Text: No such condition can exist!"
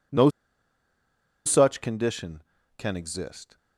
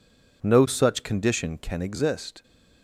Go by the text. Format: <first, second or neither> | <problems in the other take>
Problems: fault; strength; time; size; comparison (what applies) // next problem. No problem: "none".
second | pauses between "No" and "such"; at 0.2 s; 1.1 s long